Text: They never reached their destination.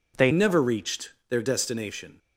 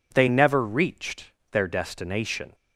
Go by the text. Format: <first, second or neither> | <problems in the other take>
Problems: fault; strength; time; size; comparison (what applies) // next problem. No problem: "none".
second | changes voice at "never"; from 0.3 s on; 1.8 s long // pauses between "reached" and "their"; slight; at 1.1 s; 0.18 s long; slight in the second